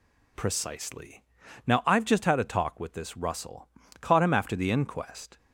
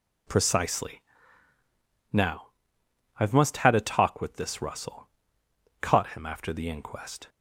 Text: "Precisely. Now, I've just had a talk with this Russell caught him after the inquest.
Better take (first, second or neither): first